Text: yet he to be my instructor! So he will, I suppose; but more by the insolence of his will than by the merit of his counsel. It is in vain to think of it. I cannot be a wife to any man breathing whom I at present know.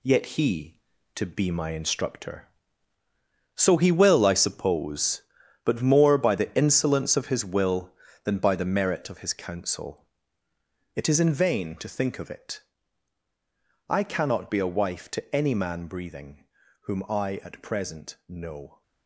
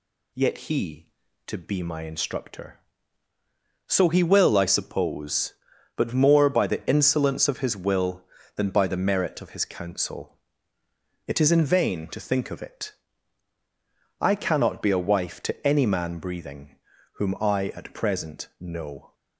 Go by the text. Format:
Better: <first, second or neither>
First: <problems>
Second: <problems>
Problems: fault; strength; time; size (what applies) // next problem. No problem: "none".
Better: second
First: gets quieter; strong; throughout; 8 dB // pauses between "breathing" and "whom"; at 16.4 s; 0.42 s long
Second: pauses between "breathing" and "whom"; at 16.7 s; 0.42 s long